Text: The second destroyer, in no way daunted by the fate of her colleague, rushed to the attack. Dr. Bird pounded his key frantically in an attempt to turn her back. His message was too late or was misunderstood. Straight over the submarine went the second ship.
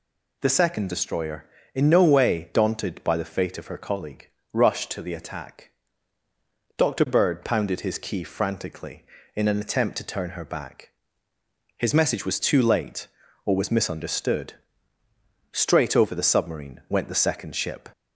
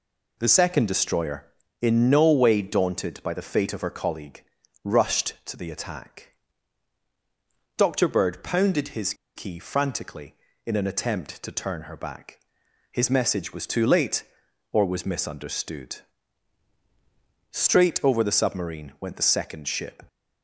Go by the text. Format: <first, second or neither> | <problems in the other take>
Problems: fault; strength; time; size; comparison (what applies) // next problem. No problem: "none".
first | pauses between "his" and "key"; slight; at 9.1 s; 0.22 s long